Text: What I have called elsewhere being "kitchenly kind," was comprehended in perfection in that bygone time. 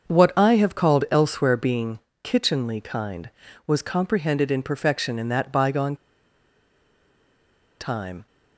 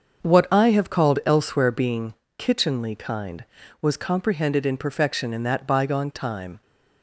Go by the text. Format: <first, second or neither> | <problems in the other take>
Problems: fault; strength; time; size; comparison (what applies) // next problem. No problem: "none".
second | starts louder than the rest; until 1.1 s; 6.5 dB; also in the second // pauses between "being" and "kitchenly"; slight; at 1.9 s; 0.24 s long; slight in the second // pauses between "bygone" and "time"; strong; at 5.9 s; 1.8 s long